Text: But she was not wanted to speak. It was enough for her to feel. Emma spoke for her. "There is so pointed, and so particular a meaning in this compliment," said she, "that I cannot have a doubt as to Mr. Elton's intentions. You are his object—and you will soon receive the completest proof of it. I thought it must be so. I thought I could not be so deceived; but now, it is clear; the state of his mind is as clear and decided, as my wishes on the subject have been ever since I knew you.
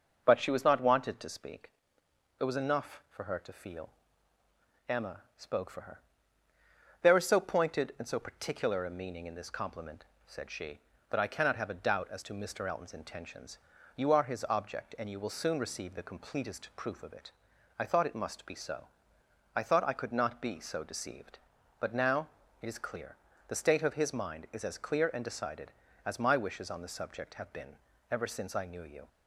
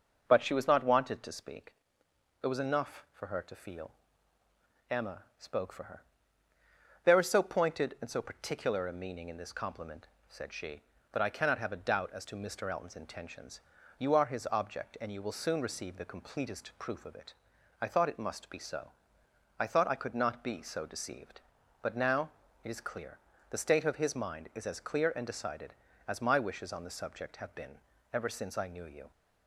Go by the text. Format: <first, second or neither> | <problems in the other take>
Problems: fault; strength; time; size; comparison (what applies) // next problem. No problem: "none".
neither | starts louder than the rest; noticeable; the same in both // pauses between "Emma" and "spoke"; slight; the same in both // pauses between "been" and "ever"; slight; the same in both